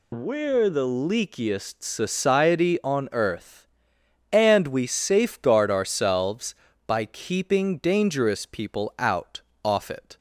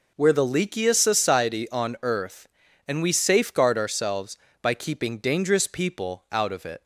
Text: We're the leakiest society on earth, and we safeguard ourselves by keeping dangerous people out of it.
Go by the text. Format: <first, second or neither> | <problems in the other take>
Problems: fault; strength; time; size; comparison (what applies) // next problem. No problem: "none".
second | says "off" for "of"; at 9.6 s